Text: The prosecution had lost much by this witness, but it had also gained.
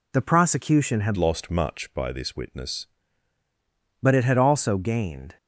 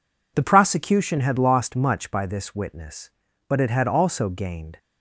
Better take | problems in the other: second | changes voice from "lost" to "witness"; from 1.1 to 2.8 s; 1.7 s long

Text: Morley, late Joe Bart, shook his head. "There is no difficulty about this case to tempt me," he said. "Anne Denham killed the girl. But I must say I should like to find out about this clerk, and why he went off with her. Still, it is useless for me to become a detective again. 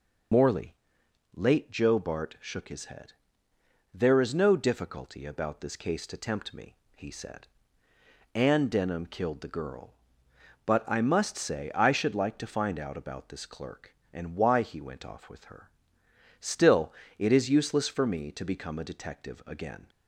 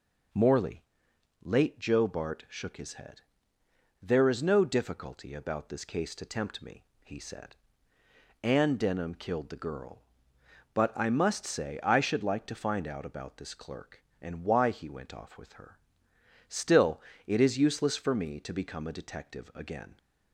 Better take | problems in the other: second | loses the start of "Morley"; at 0.3 s; 65 ms

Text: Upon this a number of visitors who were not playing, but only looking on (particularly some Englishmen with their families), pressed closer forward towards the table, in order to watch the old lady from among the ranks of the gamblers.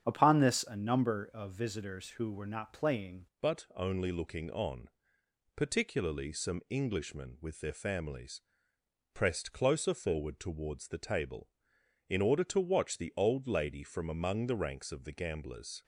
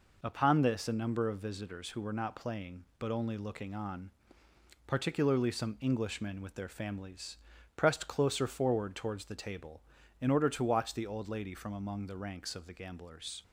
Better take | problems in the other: second | starts louder than the rest; strong; until 1.0 s; 8 dB // changes voice at "but"; from 3.4 s on; 12.4 s long

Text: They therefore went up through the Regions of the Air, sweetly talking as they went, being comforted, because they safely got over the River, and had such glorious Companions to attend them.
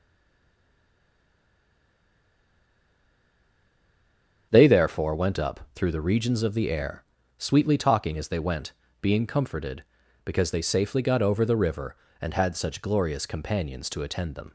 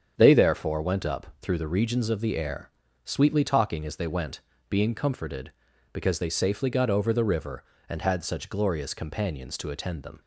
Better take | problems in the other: second | stays silent before the first word; strong; until 4.5 s; 4.5 s long // starts louder than the rest; strong; until 5.5 s; 8 dB; strong in the second // pauses between "up" and "through"; slight; at 5.5 s; 0.16 s long; slight in the second

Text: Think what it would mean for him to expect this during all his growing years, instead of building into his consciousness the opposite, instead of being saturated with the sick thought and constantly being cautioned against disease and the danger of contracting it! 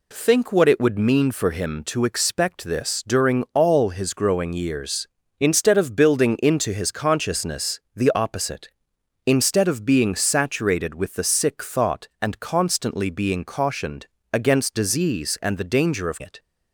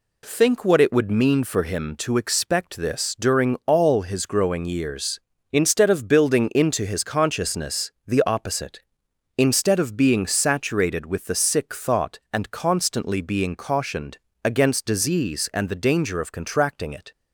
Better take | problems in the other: second | pauses between "consciousness" and "the"; slight; at 7.7 s; 0.16 s long; slight in the second // pauses between "cautioned" and "against"; slight; at 14.0 s; 0.28 s long; slight in the second // skips "contracting"; at 16.2 s

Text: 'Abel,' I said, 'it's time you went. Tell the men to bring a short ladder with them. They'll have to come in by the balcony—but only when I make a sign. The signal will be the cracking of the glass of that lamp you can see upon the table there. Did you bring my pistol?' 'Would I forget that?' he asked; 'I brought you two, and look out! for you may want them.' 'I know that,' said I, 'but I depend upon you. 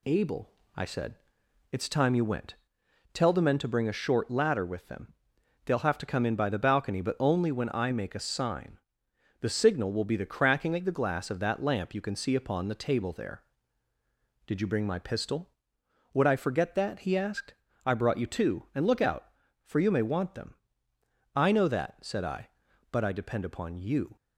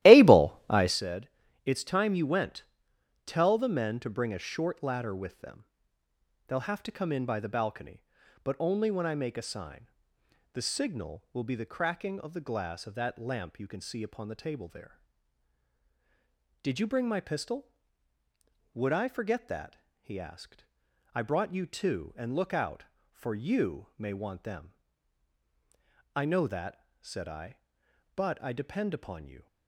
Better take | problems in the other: first | starts louder than the rest; strong; until 1.0 s; 15 dB

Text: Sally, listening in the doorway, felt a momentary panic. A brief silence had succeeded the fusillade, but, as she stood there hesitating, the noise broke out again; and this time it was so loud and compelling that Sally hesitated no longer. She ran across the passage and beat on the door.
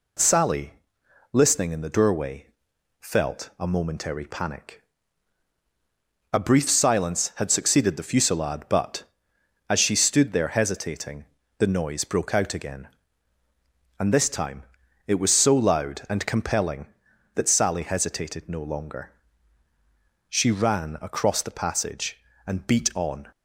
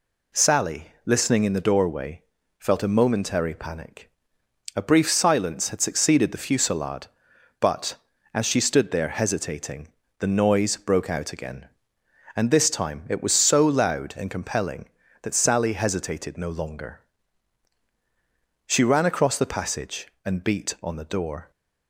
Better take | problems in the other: second | pauses between "time" and "it"; at 14.6 s; 0.42 s long // stops before "the door"; at 23.3 s

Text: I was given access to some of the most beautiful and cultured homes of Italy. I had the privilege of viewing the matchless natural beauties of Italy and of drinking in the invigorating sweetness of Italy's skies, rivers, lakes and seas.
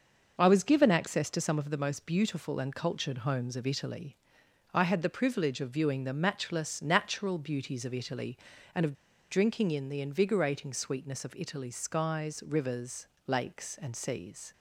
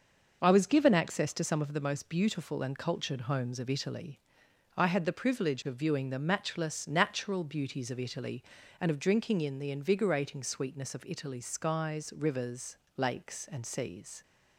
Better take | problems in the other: second | starts louder than the rest; until 1.4 s; 6 dB; also in the second // pauses between "of" and "drinking"; at 8.9 s; 0.36 s long

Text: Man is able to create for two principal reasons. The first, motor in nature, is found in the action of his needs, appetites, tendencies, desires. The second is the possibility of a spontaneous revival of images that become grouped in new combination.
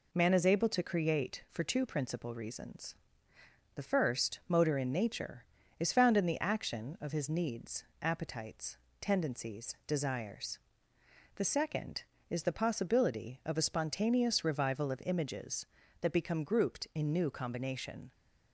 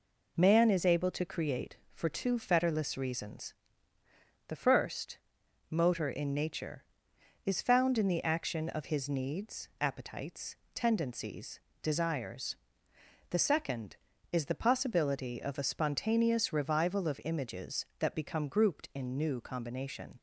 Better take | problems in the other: first | says "fetterless" for "principal"; at 2.3 s

